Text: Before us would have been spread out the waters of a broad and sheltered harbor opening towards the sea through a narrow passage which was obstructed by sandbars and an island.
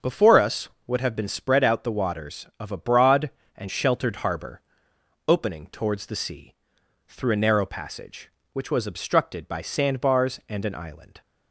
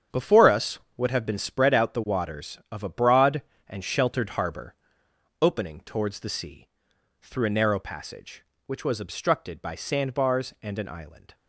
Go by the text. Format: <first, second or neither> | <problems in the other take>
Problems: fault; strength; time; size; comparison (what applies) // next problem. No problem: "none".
first | gets quieter; strong; throughout; 10 dB // starts louder than the rest; strong; until 1.3 s; 8.5 dB; also in the first // pauses between "harbor" and "opening"; noticeable; at 4.7 s; 0.66 s long; noticeable in the first // pauses between "sea" and "through"; noticeable; at 6.6 s; 0.54 s long; noticeable in the first